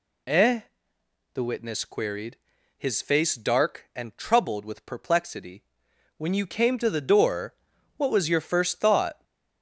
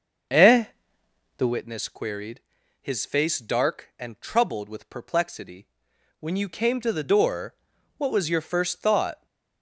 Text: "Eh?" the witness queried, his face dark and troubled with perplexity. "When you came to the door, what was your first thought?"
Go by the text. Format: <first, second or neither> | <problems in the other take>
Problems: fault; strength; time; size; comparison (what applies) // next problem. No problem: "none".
first | starts louder than the rest; until 1.6 s; 6.5 dB